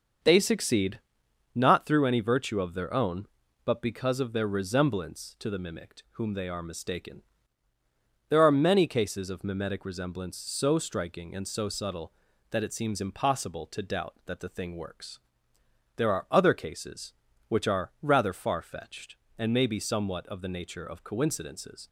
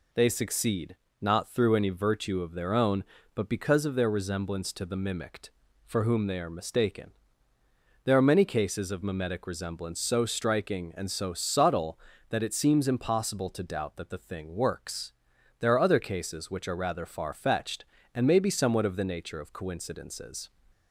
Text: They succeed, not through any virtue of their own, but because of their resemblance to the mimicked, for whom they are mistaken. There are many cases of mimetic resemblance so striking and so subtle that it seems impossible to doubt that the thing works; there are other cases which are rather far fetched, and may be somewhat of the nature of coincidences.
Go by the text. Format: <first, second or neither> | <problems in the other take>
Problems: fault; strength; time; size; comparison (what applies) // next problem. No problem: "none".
second | starts louder than the rest; until 1.7 s; 6.5 dB // skips "for"; at 6.0 s